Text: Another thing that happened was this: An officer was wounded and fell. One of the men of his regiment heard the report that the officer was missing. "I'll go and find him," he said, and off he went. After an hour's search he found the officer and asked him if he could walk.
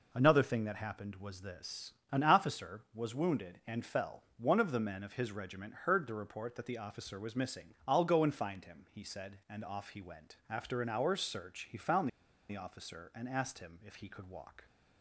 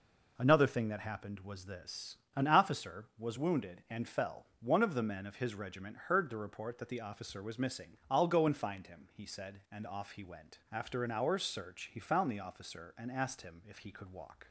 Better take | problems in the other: second | pauses between "found" and "the"; at 12.0 s; 0.39 s long

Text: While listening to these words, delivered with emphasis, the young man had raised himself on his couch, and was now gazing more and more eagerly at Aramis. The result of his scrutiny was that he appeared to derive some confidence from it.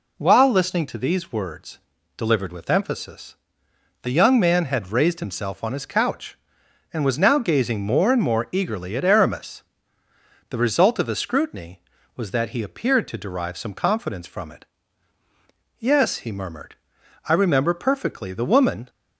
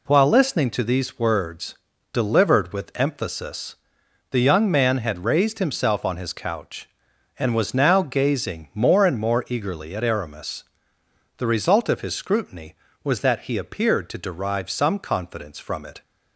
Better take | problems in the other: second | goes on to say "Yes he murmured I remember perfectly The woman"; strong; from 15.7 s on; 3.1 s long

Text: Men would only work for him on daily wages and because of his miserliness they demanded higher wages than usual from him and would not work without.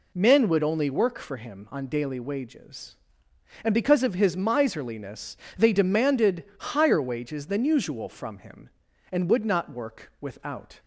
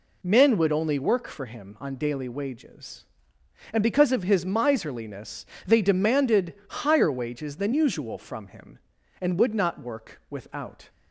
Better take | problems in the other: neither | pauses between "miserliness" and "they"; slight; the same in both // pauses between "demanded" and "higher"; slight; the same in both

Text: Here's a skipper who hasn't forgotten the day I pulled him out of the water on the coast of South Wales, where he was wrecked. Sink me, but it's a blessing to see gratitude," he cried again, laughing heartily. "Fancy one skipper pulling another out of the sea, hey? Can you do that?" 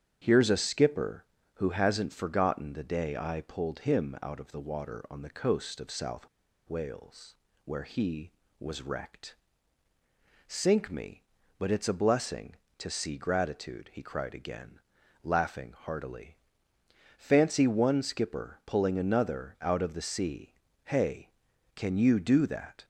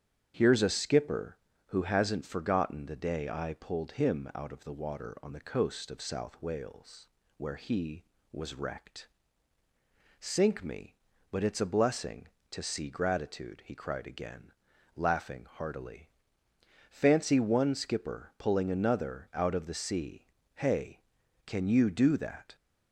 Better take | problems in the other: second | starts louder than the rest; strong; until 1.2 s; 8 dB; strong in the second // pauses between "South" and "Wales"; at 6.2 s; 0.42 s long

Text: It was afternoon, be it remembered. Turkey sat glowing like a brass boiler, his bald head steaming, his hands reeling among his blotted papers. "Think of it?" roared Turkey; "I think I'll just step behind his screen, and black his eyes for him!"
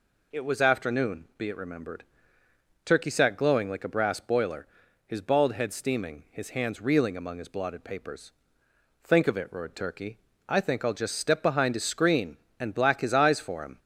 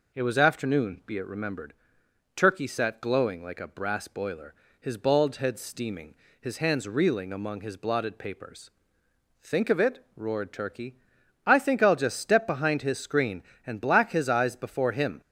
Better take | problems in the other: first | says "before" for "for"; at 14.5 s

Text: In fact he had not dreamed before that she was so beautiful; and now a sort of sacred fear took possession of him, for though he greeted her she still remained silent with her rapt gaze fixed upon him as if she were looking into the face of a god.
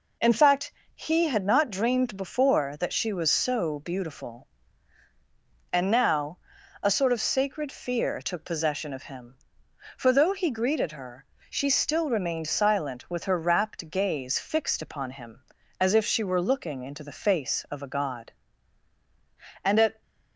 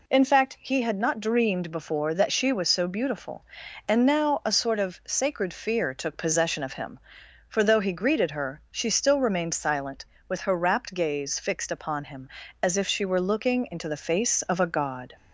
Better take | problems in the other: second | pauses between "fact" and "he"; slight; at 0.7 s; 0.24 s long // pauses between "now" and "a"; at 6.3 s; 0.44 s long // pauses between "her" and "she"; slight; at 11.2 s; 0.28 s long // goes on to say "And at"; slight; from 19.6 s on; 0.38 s long

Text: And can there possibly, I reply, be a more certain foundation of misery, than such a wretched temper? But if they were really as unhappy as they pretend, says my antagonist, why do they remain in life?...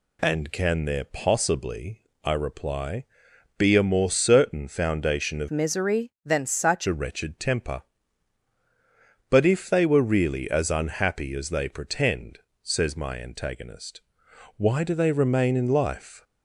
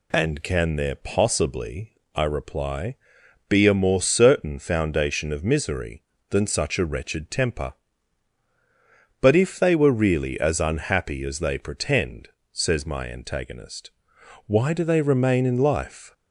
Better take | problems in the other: second | changes voice from "misery" to "such"; from 5.5 to 6.8 s; 1.3 s long

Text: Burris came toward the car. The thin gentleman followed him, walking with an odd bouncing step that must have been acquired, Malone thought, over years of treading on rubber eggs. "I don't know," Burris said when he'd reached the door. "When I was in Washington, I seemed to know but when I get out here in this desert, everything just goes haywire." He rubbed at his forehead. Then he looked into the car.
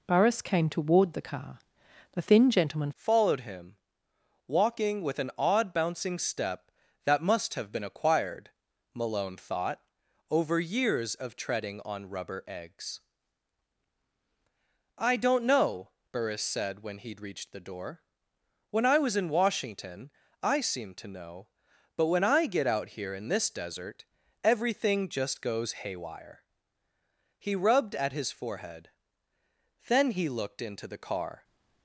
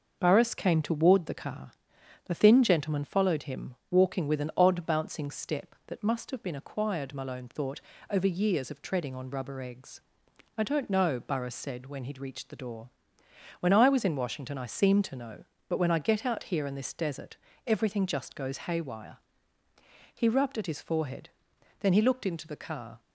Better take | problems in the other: second | changes voice at "followed"; from 2.9 s on; 28.5 s long

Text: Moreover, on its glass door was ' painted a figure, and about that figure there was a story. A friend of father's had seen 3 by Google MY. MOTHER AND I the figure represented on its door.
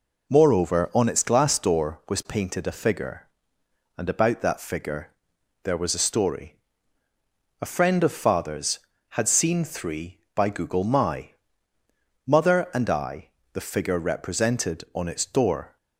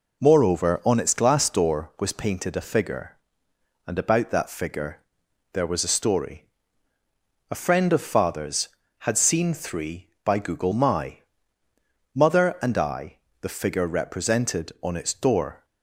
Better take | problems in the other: neither | pauses between "figure" and "there"; noticeable; the same in both // pauses between "I" and "the"; slight; the same in both

